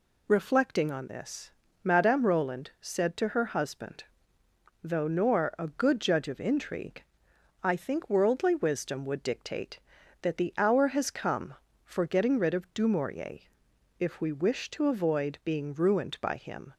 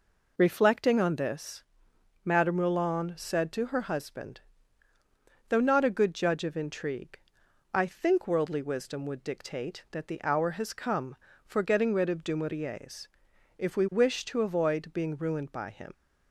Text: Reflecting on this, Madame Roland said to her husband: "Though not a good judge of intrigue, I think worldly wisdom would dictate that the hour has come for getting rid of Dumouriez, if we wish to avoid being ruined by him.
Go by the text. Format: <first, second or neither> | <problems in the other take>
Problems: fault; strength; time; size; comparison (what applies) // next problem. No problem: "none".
second | says "nor" for "not"; at 5.0 s